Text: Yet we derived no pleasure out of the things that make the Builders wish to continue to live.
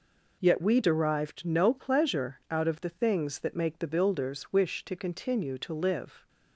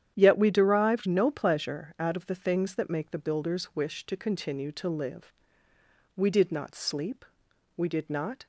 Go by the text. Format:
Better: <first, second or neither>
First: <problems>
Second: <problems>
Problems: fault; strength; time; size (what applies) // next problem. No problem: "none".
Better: first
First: none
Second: starts louder than the rest; strong; until 1.1 s; 9.5 dB // goes on to say "We did not sleep we did not"; strong; from 6.1 s on; 2.2 s long